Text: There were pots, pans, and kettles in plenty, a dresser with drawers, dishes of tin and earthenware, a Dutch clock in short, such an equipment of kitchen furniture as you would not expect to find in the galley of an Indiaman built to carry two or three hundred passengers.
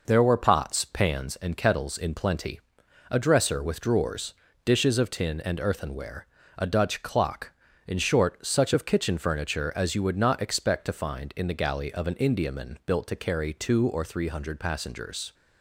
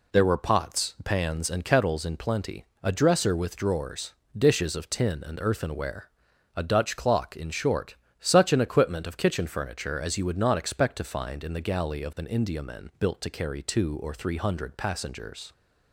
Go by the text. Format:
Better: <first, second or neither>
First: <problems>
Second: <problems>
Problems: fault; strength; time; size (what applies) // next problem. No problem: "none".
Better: second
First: skips "an equipment"; at 8.7 s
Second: none